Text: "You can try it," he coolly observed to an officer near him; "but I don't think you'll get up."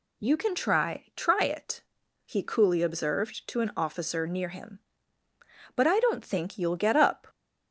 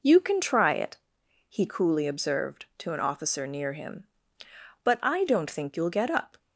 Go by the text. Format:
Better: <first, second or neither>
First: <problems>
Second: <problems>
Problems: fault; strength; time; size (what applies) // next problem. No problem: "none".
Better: second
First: says "try" twice; at 1.1 s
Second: none